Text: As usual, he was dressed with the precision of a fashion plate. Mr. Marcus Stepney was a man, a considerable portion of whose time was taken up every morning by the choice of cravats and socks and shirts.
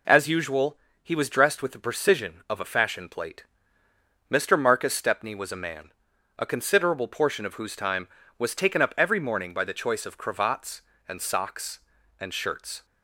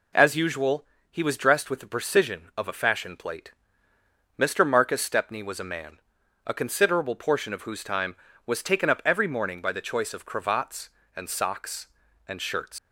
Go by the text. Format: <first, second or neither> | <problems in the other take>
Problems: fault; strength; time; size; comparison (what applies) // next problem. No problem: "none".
first | leaves "shirts" unfinished; at 12.7 s; 145 ms